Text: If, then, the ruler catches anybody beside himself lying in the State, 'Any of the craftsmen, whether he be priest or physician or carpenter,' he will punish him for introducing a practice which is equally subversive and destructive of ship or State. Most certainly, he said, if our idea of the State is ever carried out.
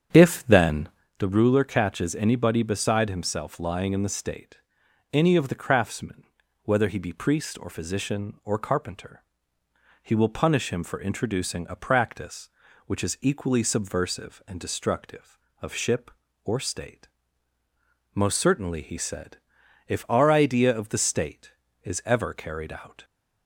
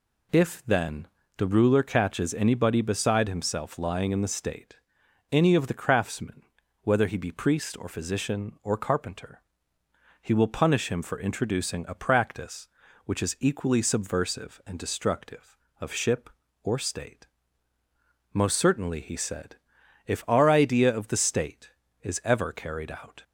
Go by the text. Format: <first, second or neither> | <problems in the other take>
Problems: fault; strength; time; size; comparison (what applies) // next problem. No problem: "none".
second | starts louder than the rest; strong; until 1.1 s; 8.5 dB